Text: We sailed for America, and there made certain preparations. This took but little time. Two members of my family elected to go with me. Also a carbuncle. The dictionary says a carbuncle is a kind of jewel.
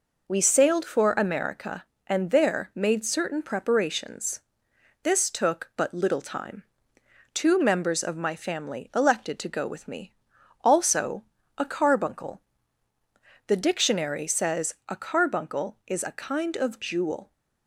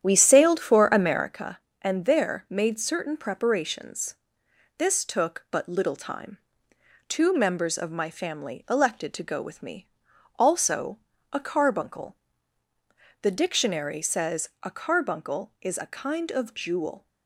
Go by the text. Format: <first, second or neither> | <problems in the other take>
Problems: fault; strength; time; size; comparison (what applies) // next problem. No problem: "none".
first | starts louder than the rest; strong; until 1.4 s; 9.5 dB // pauses between "Also" and "a"; slight; at 10.9 s; 0.36 s long; slight in the first